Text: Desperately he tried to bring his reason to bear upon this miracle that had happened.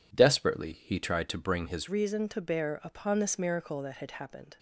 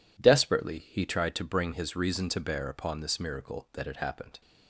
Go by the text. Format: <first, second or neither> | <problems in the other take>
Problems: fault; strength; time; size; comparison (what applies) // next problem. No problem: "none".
second | changes voice at "reason"; from 1.8 s on; 2.7 s long